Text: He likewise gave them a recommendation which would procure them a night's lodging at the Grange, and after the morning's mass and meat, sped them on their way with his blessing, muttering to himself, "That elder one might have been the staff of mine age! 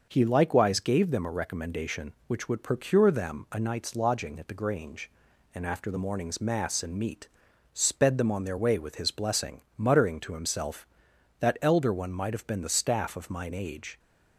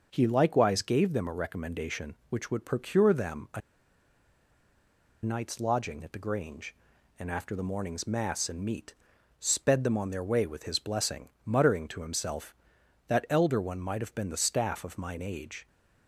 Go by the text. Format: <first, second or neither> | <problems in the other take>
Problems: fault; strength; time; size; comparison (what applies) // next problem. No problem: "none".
first | starts louder than the rest; noticeable; until 1.1 s; 6 dB; noticeable in the first // pauses between "a" and "night's"; strong; at 3.6 s; 1.6 s long